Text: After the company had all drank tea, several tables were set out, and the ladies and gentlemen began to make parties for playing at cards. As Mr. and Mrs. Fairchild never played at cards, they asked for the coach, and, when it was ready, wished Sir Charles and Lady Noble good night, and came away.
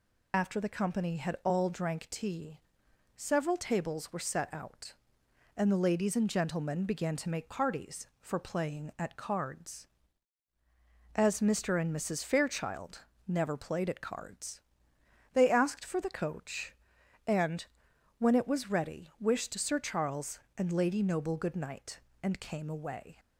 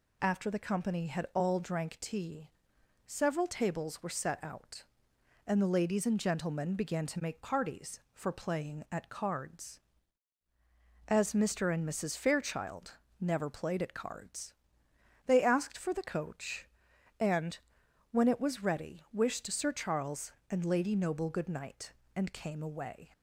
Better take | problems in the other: second | loses the start of "After"; at 0.3 s; 30 ms // pauses between "Fairchild" and "never"; slight; at 13.0 s; 0.28 s long; slight in the second

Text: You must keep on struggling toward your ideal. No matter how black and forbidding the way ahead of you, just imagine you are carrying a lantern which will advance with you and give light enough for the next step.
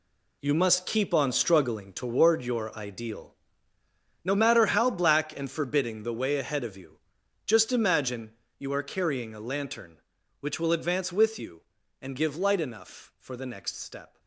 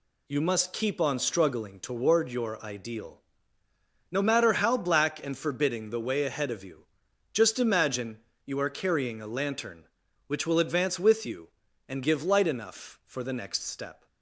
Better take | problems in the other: second | gets quieter; strong; throughout; 10.5 dB // pauses between "imagine" and "you"; slight; at 8.3 s; 0.26 s long; slight in the second

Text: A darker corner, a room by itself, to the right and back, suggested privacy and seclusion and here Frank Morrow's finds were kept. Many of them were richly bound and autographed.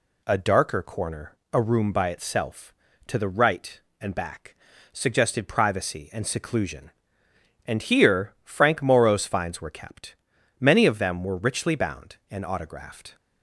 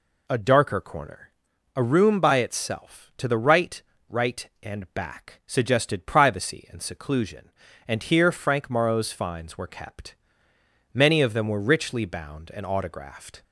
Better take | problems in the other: first | says "right" twice; at 4.0 s

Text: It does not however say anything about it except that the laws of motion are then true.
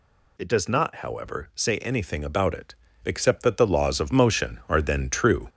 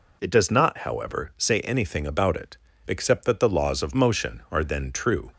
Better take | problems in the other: second | gets louder; slight; throughout; 3.5 dB // pauses between "it" and "except"; slight; at 2.7 s; 0.30 s long; slight in the second

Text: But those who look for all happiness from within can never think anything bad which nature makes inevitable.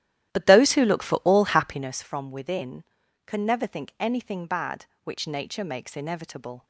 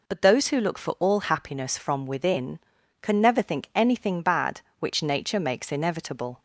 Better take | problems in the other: second | starts louder than the rest; strong; until 2.0 s; 12.5 dB

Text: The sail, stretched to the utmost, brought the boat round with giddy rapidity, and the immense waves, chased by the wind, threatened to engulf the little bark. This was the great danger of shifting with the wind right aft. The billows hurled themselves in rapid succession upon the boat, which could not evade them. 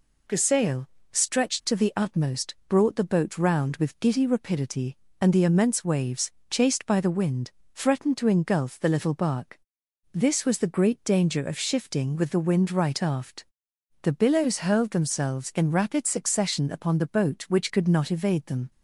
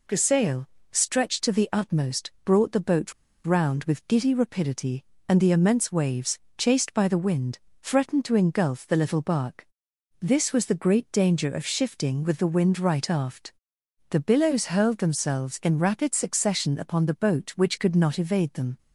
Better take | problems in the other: first | pauses between "boat" and "round"; slight; at 3.1 s; 0.32 s long

